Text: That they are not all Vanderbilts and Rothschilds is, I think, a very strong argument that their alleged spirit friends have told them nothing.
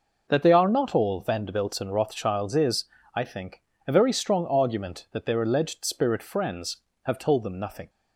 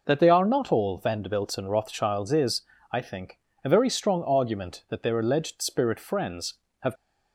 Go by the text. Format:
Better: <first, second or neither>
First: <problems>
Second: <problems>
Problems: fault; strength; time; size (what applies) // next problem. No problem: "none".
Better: first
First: none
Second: stops before "told them nothing"; at 6.9 s